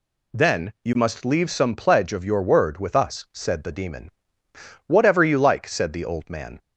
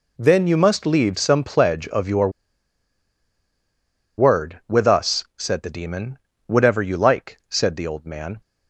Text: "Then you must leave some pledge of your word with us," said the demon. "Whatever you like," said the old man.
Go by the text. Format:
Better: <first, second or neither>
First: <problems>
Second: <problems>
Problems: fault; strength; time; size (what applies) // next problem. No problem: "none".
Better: first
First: none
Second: pauses between "your" and "word"; strong; at 2.3 s; 1.8 s long